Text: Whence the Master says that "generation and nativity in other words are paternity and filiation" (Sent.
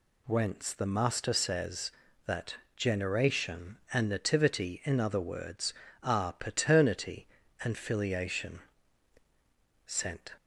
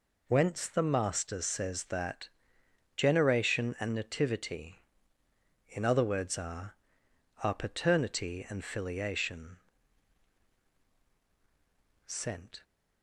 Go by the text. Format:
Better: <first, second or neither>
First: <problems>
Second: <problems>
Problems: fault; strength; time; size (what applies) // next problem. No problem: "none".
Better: first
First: pauses between "that" and "generation"; slight; at 2.5 s; 0.22 s long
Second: pauses between "that" and "generation"; noticeable; at 2.3 s; 0.66 s long // says "are" twice; at 7.4 s